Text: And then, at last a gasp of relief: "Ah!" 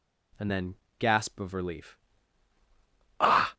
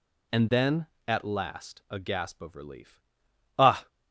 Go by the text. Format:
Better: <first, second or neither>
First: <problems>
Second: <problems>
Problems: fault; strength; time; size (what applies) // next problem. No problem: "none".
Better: second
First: skips "at last a"; at 0.8 s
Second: none